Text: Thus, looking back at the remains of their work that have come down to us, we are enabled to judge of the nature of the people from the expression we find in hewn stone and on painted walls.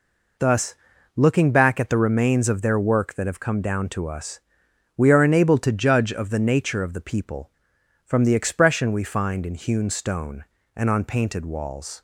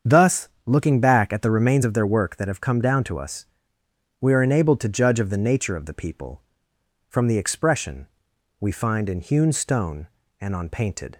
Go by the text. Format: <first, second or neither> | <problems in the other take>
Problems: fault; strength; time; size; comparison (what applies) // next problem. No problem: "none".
first | starts louder than the rest; strong; until 1.2 s; 7.5 dB // pauses between "expression" and "we"; noticeable; at 8.0 s; 0.54 s long // stops before "walls"; at 11.1 s